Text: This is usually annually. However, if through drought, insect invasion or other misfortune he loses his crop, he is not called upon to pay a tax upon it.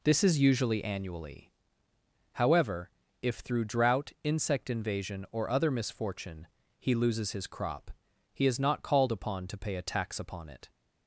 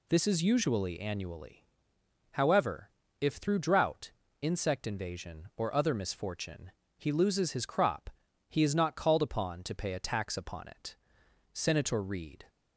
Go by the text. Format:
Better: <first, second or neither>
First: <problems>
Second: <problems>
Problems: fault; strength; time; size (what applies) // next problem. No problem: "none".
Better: first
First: pauses between "misfortune" and "he"; slight; at 6.4 s; 0.32 s long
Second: pauses between "misfortune" and "he"; slight; at 6.7 s; 0.26 s long // goes on to say "SENATOR REED"; noticeable; from 11.5 s on; 0.96 s long